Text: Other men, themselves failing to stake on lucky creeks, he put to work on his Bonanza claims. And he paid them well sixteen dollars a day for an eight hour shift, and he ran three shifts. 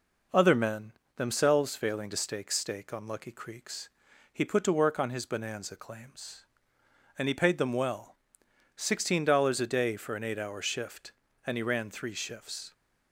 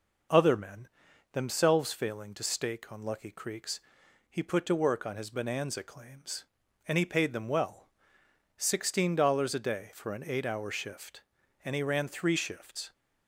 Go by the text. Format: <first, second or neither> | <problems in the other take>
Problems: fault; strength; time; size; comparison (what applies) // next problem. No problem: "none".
second | says "stake" twice; at 2.5 s // pauses between "well" and "sixteen"; noticeable; at 8.1 s; 0.60 s long; noticeable in the second